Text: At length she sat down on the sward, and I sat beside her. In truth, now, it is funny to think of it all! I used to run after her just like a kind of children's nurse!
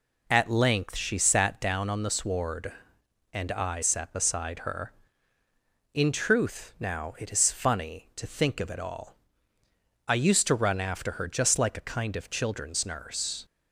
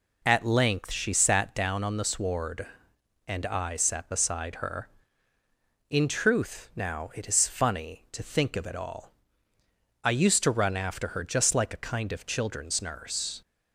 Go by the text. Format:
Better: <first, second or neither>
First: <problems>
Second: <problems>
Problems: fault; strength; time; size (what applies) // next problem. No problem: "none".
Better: neither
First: none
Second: none